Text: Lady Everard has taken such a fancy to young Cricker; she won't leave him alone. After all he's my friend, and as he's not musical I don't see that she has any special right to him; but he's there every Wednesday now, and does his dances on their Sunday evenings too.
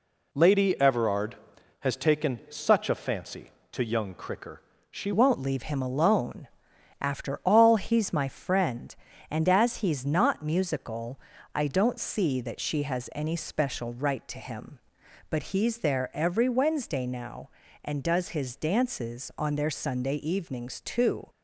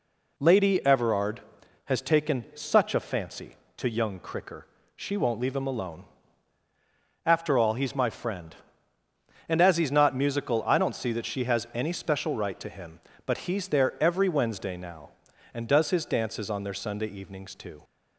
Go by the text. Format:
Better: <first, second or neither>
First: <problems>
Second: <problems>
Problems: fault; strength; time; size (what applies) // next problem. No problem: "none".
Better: second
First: changes voice at "won't"; from 5.1 s on; 16.1 s long // pauses between "musical" and "I"; slight; at 11.2 s; 0.34 s long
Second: none